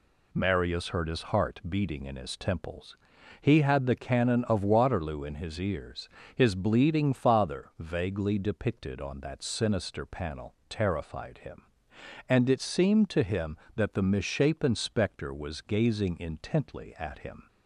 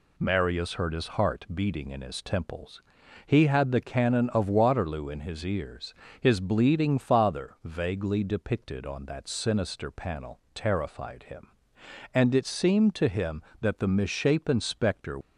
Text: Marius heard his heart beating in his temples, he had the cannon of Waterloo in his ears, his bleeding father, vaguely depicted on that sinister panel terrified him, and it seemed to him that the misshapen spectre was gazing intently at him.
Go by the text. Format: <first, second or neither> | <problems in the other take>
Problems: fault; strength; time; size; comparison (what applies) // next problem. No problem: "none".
first | pauses between "panel" and "terrified"; slight; at 10.3 s; 0.16 s long; slight in the first // stops before "was gazing intently at him"; at 15.2 s